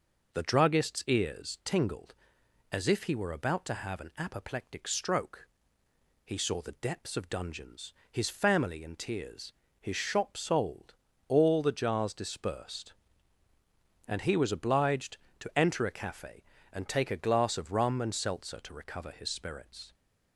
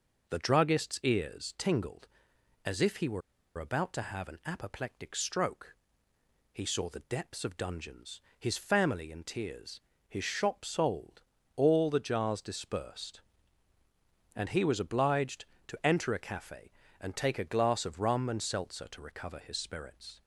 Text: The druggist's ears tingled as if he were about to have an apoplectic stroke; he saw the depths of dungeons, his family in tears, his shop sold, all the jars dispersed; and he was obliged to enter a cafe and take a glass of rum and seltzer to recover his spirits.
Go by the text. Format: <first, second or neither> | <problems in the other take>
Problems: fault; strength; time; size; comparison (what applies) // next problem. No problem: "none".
first | pauses between "were" and "about"; at 3.2 s; 0.36 s long